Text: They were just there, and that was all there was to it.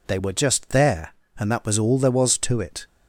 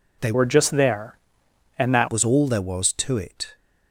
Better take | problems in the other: first | changes voice from "were" to "that"; from 0.3 to 2.0 s; 1.7 s long

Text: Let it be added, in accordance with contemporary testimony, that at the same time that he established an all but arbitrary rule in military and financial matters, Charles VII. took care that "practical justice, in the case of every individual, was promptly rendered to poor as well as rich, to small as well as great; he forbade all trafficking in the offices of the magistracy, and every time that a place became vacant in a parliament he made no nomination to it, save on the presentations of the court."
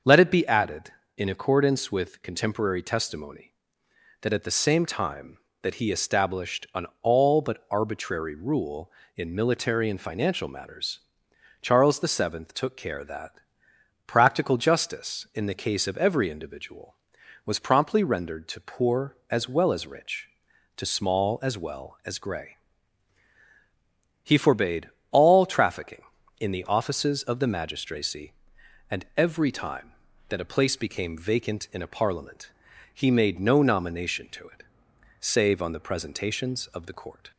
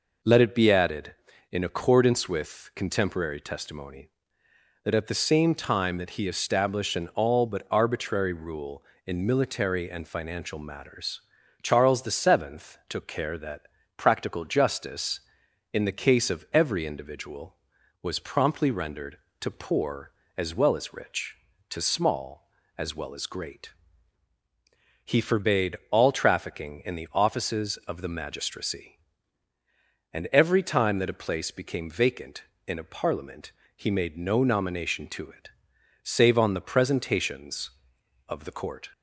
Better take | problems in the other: second | starts louder than the rest; until 1.3 s; 6.5 dB // pauses between "that" and "practical"; noticeable; at 13.4 s; 0.66 s long; slight in the second // says "grey" for "great"; at 22.1 s // pauses between "forbade" and "all"; slight; at 24.8 s; 0.22 s long // pauses between "parliament" and "he"; at 32.5 s; 0.42 s long; slight in the second

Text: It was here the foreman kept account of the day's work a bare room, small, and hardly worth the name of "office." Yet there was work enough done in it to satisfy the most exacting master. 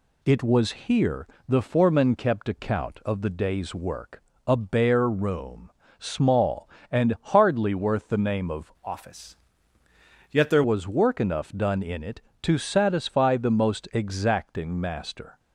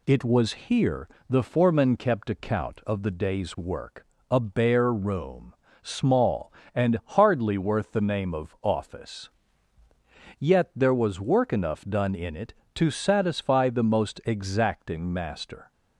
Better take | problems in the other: second | pauses between "here" and "the"; slight; at 1.2 s; 0.22 s long; slight in the second // pauses between "work" and "a"; slight; at 4.2 s; 0.24 s long; slight in the second // changes voice from "office" to "there"; from 8.8 to 10.6 s; 1.8 s long

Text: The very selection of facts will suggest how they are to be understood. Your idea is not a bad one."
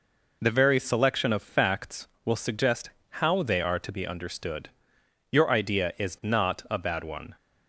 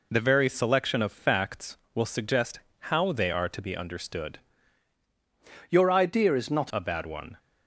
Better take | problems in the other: first | pauses between "suggest" and "how"; slight; at 2.5 s; 0.32 s long; slight in the first // changes voice from "Your" to "not"; from 5.6 to 6.7 s; 1.1 s long

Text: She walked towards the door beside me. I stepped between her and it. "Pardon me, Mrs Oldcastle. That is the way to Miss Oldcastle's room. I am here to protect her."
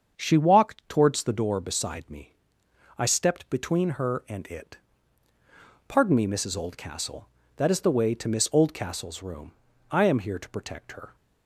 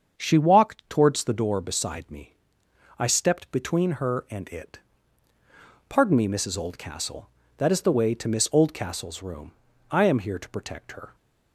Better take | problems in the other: neither | starts louder than the rest; the same in both

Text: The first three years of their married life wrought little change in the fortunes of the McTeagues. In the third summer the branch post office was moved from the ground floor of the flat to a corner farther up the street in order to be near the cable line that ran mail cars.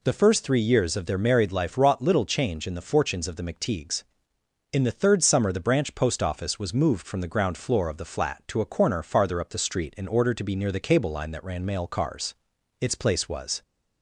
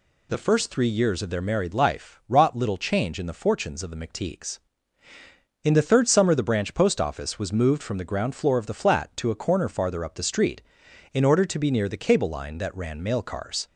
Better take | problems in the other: second | goes on to say "Its place was"; noticeable; from 12.7 s on; 0.82 s long

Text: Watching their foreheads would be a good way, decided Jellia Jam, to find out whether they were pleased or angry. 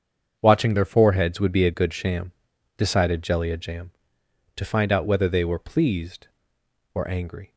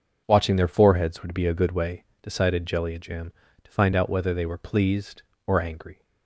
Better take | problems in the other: second | starts louder than the rest; strong; until 1.4 s; 7 dB // says "sham" for "way"; at 1.9 s

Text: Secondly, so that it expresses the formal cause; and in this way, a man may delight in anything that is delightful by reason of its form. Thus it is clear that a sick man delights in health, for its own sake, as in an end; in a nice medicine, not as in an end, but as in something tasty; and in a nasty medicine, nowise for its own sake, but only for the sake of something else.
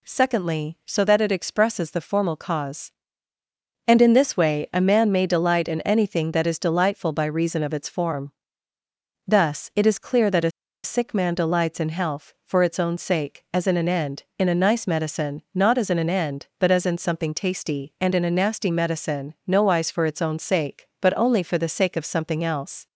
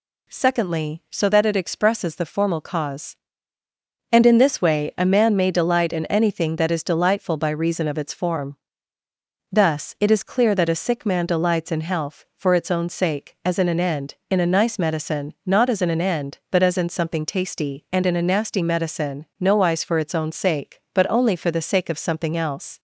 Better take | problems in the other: second | pauses between "a" and "sick"; slight; at 10.4 s; 0.34 s long

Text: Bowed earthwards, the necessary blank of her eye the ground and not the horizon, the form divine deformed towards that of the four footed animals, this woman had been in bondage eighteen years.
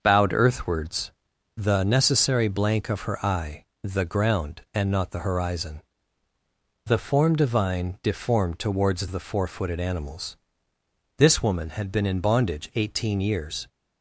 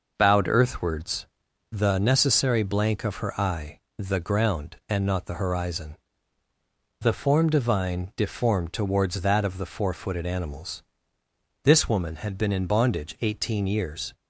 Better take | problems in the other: second | starts louder than the rest; until 1.0 s; 6 dB // pauses between "eye" and "the"; slight; at 3.6 s; 0.18 s long; slight in the second // skips "that of"; at 9.0 s

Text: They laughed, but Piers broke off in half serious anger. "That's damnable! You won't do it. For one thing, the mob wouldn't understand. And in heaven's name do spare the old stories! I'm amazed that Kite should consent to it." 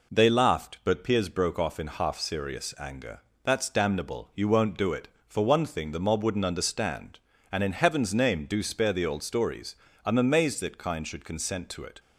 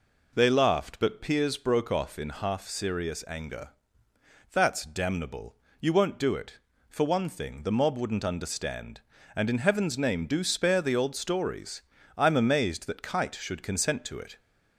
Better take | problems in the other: second | says "Kind" for "Kite"; at 10.7 s

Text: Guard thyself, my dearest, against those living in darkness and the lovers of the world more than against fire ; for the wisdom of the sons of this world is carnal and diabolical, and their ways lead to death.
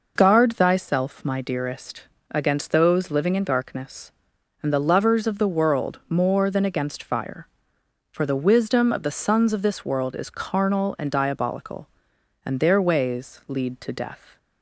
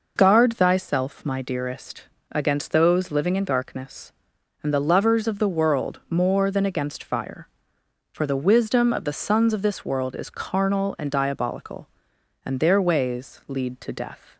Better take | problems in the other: neither | none

